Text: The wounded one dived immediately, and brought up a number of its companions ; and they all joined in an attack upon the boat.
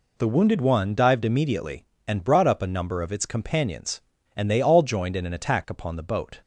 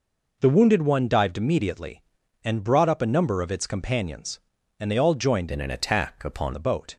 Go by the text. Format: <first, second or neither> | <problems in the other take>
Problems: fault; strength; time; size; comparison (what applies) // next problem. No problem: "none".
first | changes voice from "in" to "upon"; from 5.4 to 6.5 s; 1.1 s long